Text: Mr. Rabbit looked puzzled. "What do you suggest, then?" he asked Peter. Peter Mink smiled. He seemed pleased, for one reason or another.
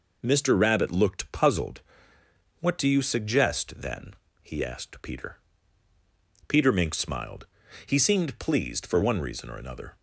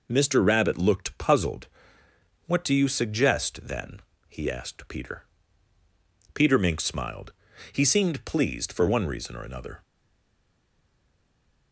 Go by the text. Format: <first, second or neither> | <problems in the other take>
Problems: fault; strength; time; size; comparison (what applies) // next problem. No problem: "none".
first | stays silent after the last word; noticeable; from 9.8 s on; 1.9 s long